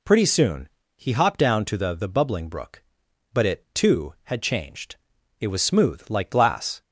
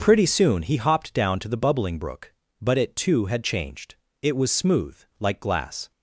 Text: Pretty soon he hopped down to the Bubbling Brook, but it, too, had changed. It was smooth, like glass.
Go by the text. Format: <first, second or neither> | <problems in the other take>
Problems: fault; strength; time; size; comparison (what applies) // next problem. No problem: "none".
second | pauses between "soon" and "he"; slight; at 0.6 s; 0.28 s long // says "the" twice; at 1.9 s